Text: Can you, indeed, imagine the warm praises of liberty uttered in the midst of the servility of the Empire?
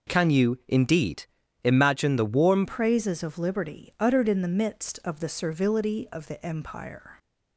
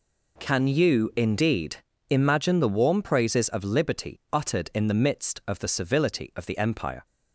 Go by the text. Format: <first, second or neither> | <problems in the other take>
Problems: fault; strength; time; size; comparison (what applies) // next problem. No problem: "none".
second | changes voice at "praises"; from 2.6 s on; 4.5 s long